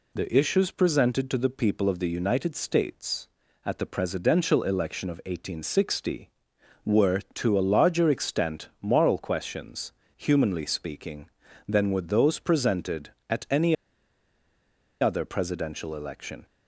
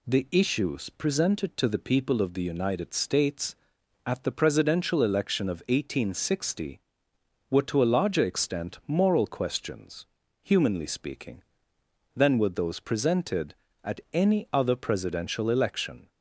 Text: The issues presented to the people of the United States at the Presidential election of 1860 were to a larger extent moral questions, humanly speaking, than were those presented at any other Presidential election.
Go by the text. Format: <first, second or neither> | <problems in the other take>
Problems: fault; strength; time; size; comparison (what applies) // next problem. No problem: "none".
second | pauses between "any" and "other"; strong; at 13.7 s; 1.2 s long